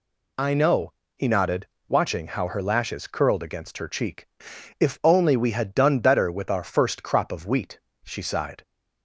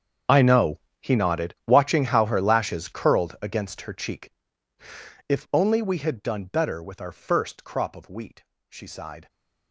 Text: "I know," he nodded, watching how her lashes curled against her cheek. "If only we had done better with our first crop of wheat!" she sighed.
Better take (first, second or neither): first